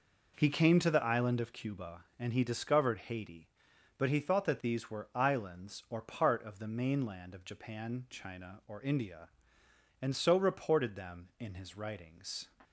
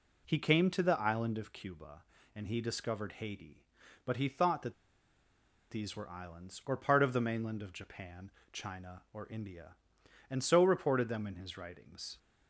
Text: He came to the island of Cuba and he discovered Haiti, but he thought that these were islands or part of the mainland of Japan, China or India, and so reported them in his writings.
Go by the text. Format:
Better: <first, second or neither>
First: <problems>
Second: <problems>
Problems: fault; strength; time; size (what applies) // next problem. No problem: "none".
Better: first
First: none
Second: pauses between "that" and "these"; noticeable; at 4.7 s; 0.96 s long